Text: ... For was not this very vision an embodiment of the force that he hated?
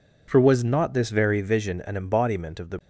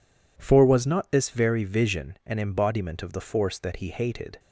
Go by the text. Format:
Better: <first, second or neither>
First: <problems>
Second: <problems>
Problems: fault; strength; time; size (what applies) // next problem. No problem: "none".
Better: second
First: stops before "force that he hated"; at 2.7 s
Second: none